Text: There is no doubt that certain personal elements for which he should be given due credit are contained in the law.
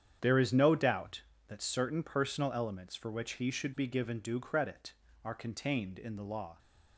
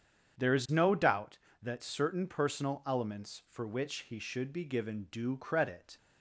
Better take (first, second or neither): first